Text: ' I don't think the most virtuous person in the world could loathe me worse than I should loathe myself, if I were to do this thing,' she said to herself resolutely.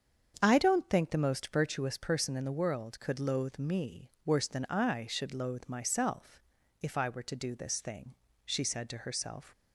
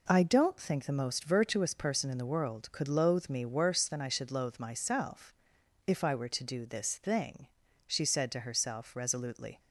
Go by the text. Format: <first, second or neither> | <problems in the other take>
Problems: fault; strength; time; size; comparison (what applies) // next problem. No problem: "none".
second | starts louder than the rest; strong; until 1.3 s; 7.5 dB // stops before "resolutely"; at 9.5 s